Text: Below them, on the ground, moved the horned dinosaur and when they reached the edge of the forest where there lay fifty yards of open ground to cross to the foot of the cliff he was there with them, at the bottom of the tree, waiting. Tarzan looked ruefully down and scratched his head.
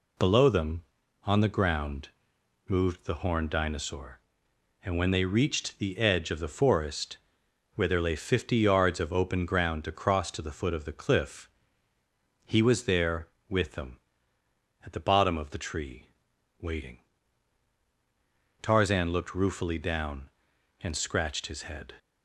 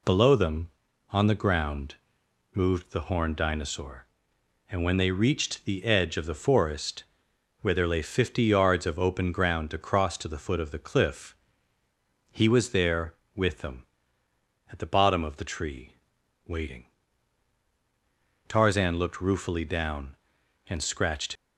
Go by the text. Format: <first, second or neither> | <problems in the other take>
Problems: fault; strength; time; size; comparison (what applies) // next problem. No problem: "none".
first | pauses between "forest" and "where"; noticeable; at 7.0 s; 0.56 s long; noticeable in the first // pauses between "cliff" and "he"; noticeable; at 11.3 s; 0.96 s long; noticeable in the first // stops before "his head"; at 21.3 s